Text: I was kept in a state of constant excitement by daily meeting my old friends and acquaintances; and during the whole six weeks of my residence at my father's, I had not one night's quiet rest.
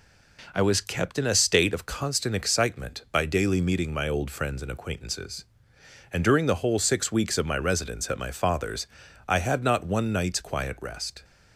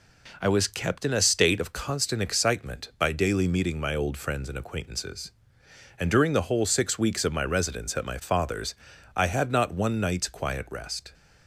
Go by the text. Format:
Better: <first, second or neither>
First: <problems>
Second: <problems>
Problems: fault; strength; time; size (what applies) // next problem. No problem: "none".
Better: neither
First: none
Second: none